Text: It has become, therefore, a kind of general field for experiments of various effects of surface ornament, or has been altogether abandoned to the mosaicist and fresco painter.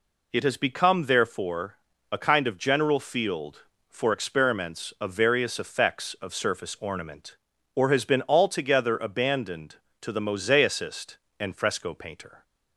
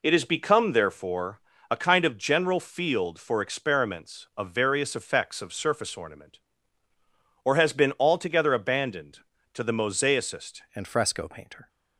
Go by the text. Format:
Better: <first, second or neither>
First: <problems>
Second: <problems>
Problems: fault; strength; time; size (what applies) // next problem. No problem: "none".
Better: first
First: none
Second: changes voice at "and"; from 10.7 s on; 0.9 s long